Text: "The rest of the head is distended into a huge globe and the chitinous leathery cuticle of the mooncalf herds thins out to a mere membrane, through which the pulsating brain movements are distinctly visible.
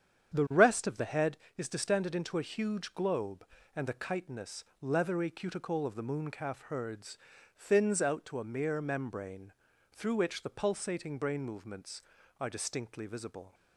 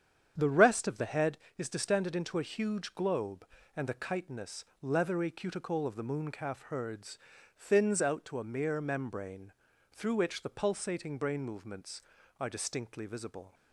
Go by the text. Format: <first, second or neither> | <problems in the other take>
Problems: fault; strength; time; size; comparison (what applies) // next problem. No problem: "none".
neither | starts louder than the rest; strong; the same in both // pauses between "chitinous" and "leathery"; slight; the same in both // pauses between "herds" and "thins"; the same in both